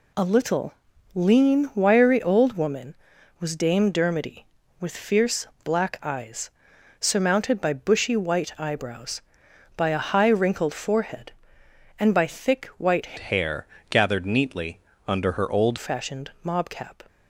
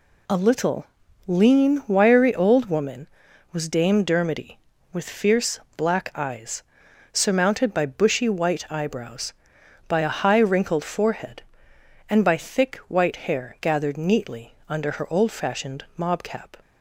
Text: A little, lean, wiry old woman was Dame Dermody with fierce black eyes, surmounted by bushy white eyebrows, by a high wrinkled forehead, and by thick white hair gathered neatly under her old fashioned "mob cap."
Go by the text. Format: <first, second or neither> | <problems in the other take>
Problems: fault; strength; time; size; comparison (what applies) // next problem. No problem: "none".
second | pauses between "fierce" and "black"; slight; at 5.4 s; 0.16 s long; slight in the second // changes voice from "hair" to "old"; from 13.1 to 15.7 s; 2.6 s long // pauses between "hair" and "gathered"; slight; at 13.6 s; 0.24 s long // pauses between "neatly" and "under"; slight; at 14.7 s; 0.30 s long; slight in the second